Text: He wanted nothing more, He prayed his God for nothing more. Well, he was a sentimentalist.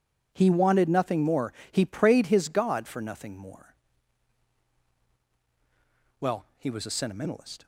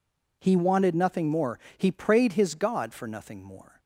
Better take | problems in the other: first | stops before "Well he was a sentimentalist"; at 3.7 s

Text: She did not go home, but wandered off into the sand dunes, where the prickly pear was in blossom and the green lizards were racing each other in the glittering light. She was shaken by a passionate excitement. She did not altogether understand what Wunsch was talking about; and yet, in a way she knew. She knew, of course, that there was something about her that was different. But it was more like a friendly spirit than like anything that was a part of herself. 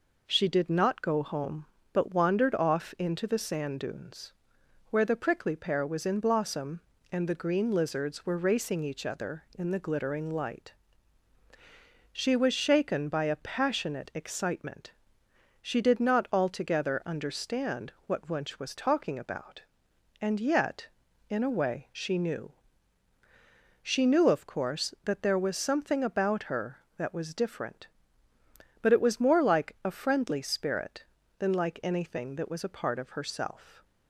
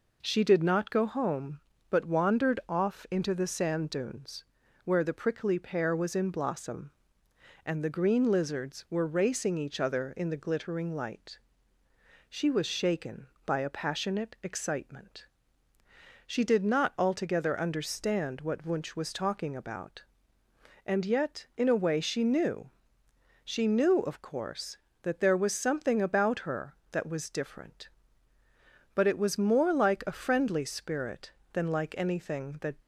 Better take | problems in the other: first | stops before "was a part of herself"; at 32.7 s

